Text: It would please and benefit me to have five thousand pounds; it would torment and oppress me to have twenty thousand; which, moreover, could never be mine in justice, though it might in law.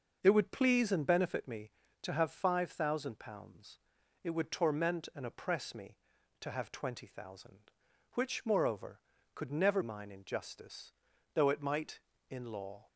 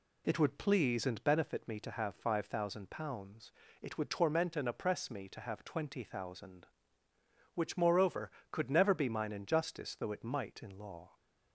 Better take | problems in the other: second | starts louder than the rest; until 1.2 s; 6 dB // skips "be"; at 9.8 s

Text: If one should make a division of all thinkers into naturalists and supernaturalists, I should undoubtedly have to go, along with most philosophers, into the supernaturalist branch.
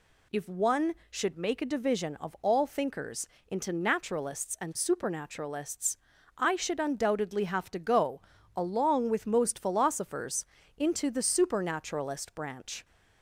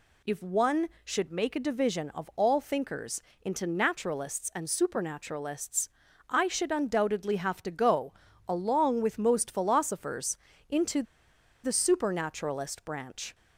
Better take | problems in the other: first | pauses between "thinkers" and "into"; slight; at 3.2 s; 0.20 s long; slight in the first // pauses between "into" and "the"; noticeable; at 11.0 s; 0.61 s long

